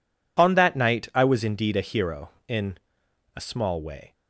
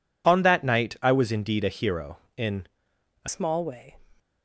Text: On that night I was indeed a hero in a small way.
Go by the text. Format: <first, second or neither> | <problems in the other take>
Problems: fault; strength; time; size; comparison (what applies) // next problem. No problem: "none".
first | pauses between "in" and "a"; noticeable; at 2.6 s; 0.58 s long; noticeable in the first // changes voice at "small"; from 3.2 s on; 0.7 s long